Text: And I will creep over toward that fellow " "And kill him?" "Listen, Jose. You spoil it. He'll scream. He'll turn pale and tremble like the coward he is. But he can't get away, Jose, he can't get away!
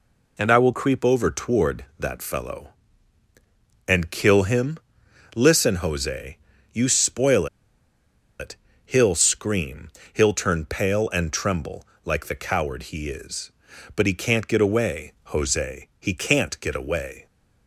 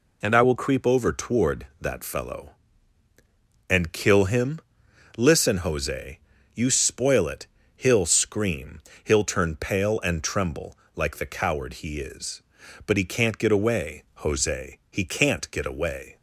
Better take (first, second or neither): second